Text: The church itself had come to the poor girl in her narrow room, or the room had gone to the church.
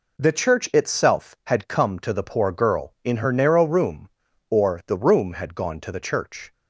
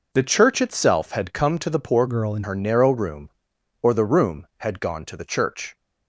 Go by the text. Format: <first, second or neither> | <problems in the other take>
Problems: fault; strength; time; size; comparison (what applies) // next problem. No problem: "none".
first | changes voice from "girl" to "in"; from 2.0 to 2.4 s; 0.4 s long